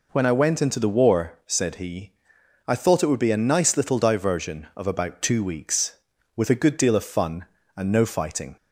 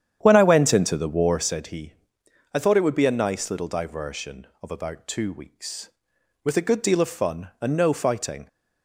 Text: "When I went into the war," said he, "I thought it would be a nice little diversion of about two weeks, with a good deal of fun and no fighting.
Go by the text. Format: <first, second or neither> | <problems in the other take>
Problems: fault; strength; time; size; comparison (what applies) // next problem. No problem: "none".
first | starts louder than the rest; strong; until 1.6 s; 9.5 dB